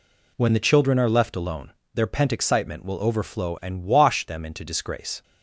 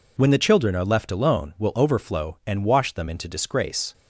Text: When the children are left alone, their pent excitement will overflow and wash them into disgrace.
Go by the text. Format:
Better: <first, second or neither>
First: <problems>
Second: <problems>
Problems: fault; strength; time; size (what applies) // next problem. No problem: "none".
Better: first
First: none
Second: skips "their pent excitement"; at 1.5 s